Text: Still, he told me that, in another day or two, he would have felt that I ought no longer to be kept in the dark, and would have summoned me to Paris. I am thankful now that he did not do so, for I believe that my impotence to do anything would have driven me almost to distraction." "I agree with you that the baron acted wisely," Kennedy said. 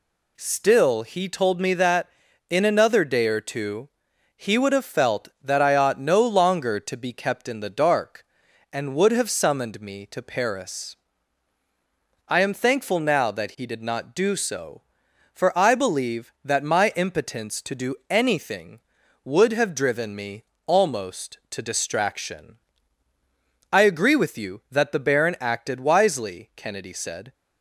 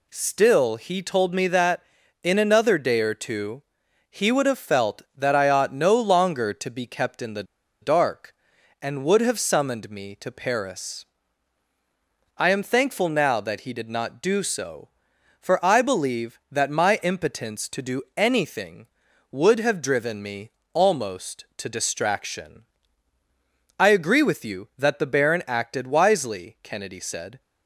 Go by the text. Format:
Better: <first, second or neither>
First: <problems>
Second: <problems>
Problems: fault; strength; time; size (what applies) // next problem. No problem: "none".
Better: first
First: pauses between "me" and "almost"; slight; at 20.4 s; 0.22 s long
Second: pauses between "the" and "dark"; at 7.4 s; 0.37 s long // pauses between "me" and "almost"; slight; at 20.5 s; 0.22 s long